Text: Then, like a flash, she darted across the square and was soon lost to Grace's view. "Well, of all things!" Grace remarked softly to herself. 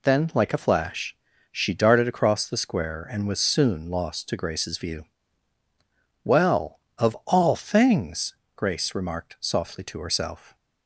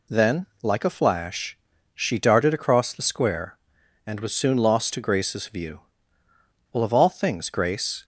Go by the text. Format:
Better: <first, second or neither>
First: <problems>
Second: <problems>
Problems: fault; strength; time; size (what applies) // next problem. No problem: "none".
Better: first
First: none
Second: stops before "remarked softly to herself"; at 8.0 s